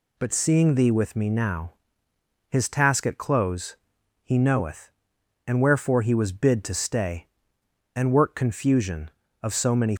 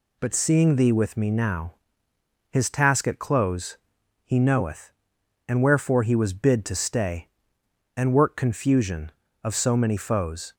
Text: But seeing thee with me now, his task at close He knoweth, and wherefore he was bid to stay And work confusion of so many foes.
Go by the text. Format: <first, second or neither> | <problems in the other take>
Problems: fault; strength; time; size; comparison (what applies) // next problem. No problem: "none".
second | pauses between "close" and "He"; noticeable; at 3.7 s; 0.48 s long; noticeable in the second // stops before "foes"; at 9.9 s